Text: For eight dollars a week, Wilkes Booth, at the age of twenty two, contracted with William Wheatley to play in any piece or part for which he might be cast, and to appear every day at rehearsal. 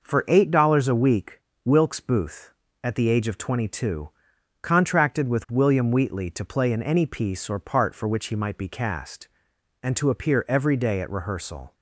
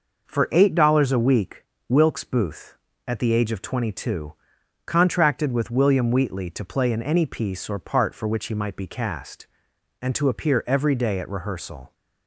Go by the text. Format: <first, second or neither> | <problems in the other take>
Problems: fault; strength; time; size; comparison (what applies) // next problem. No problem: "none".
neither | none